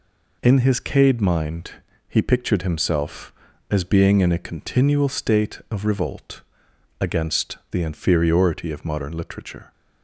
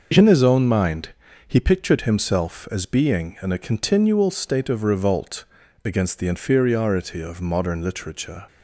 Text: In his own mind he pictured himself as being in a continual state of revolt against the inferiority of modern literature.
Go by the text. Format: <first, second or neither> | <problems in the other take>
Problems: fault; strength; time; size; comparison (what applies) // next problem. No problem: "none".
second | says "cade" for "own"; at 0.7 s // pauses between "mind" and "he"; slight; at 1.7 s; 0.34 s long; slight in the second // pauses between "revolt" and "against"; noticeable; at 6.4 s; 0.58 s long; also in the second // pauses between "against" and "the"; slight; at 7.5 s; 0.16 s long